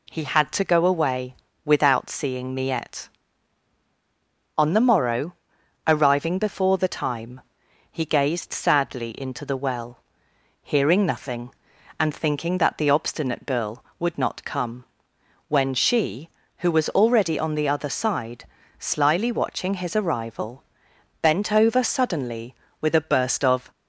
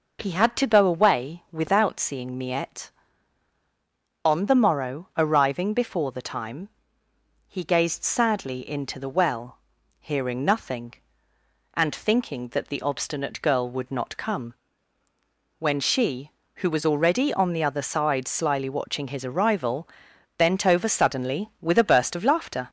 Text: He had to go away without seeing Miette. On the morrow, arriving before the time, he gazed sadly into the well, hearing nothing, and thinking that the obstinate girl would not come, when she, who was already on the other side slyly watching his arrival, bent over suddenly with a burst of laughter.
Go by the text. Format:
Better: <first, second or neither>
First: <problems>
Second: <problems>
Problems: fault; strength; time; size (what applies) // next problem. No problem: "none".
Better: second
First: pauses between "away" and "without"; slight; at 1.3 s; 0.28 s long // pauses between "side" and "slyly"; slight; at 18.4 s; 0.34 s long // stops before "laughter"; at 23.7 s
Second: none